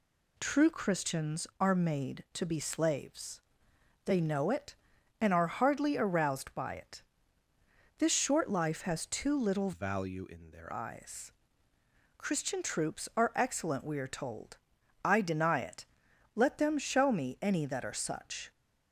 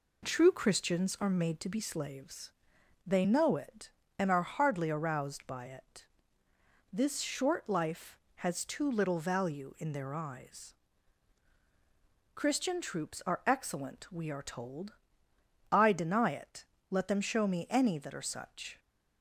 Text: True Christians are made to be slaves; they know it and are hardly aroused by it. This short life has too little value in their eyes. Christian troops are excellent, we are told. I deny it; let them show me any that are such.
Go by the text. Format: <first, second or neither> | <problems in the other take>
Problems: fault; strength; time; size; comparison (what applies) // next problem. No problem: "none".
second | changes voice from "value" to "their"; from 9.7 to 10.7 s; 1.0 s long